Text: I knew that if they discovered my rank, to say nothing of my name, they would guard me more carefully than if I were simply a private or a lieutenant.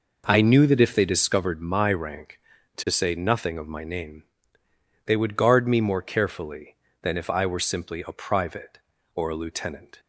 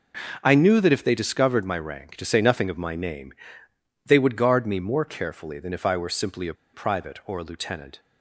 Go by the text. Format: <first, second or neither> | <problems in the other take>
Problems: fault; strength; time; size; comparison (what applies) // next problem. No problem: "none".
first | starts louder than the rest; noticeable; until 1.4 s; 6 dB // pauses between "a" and "private"; slight; at 6.5 s; 0.20 s long